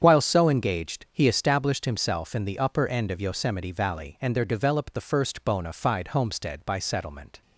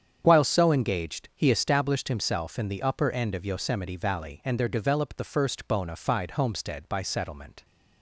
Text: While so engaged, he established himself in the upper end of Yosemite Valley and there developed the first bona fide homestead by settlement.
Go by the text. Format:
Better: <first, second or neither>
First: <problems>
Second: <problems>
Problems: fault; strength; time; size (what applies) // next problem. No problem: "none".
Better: neither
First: starts louder than the rest; strong; until 1.0 s; 8 dB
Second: starts louder than the rest; strong; until 1.2 s; 8 dB